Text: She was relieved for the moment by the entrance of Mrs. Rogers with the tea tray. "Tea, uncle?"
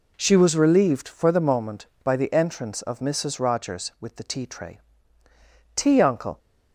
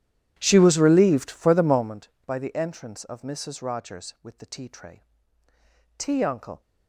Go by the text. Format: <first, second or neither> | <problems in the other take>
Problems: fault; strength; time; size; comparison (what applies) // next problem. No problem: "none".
first | starts louder than the rest; strong; until 2.0 s; 11.5 dB